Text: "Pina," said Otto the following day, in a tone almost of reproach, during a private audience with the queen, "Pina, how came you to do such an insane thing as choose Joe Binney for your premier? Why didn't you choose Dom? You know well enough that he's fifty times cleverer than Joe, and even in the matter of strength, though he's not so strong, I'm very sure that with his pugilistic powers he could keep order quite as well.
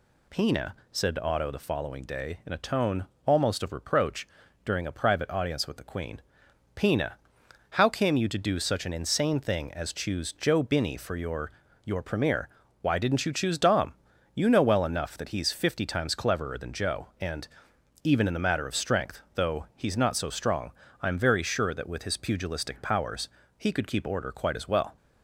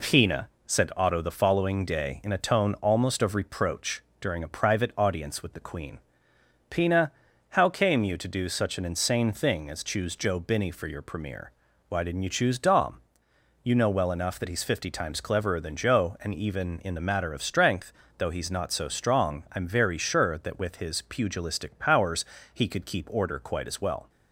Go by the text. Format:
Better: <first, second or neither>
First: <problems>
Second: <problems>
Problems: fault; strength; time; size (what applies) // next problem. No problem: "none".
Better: second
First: pauses between "tone" and "almost"; slight; at 3.0 s; 0.20 s long // says "your" twice; at 11.8 s // pauses between "and" and "even"; noticeable; at 17.4 s; 0.56 s long // pauses between "powers" and "he"; slight; at 23.2 s; 0.28 s long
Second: pauses between "powers" and "he"; slight; at 22.2 s; 0.30 s long